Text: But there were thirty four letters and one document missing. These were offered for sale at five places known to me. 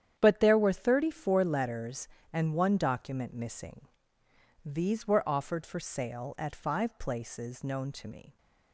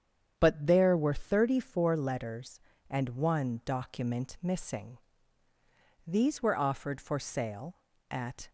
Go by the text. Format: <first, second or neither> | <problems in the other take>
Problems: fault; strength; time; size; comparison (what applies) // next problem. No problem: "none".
first | starts louder than the rest; strong; until 1.3 s; 8 dB; strong in the first // stops before "five places known to me"; at 8.4 s